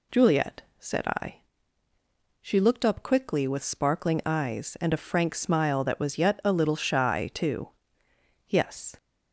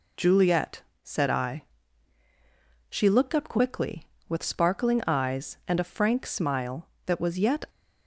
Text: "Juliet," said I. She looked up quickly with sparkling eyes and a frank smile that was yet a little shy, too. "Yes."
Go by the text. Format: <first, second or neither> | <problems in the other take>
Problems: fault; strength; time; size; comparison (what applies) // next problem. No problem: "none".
first | stops before "a little shy too Yes"; at 7.6 s